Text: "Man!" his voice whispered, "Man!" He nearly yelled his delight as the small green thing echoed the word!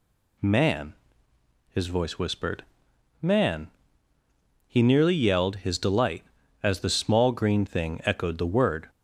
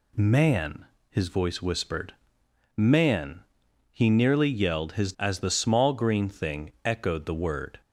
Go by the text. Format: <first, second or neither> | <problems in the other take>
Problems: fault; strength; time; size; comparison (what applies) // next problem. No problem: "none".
first | skips "delight"; at 5.1 s